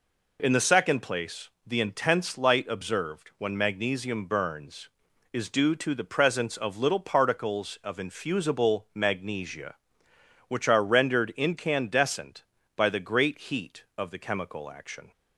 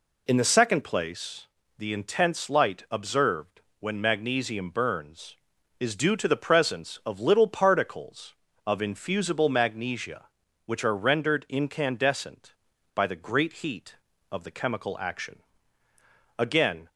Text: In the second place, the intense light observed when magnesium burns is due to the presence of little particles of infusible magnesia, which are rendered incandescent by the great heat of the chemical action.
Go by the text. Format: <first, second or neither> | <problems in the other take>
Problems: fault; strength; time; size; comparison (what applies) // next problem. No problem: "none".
first | pauses between "observed" and "when"; slight; at 3.6 s; 0.18 s long // goes on to say "Again"; from 16.3 s on; 0.50 s long